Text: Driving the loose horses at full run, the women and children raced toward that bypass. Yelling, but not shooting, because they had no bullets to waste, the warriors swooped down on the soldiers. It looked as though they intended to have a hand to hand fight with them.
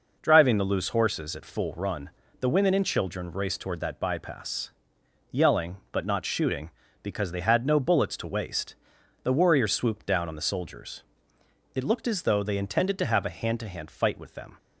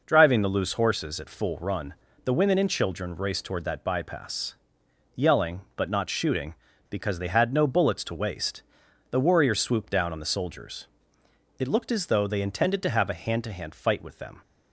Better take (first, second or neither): neither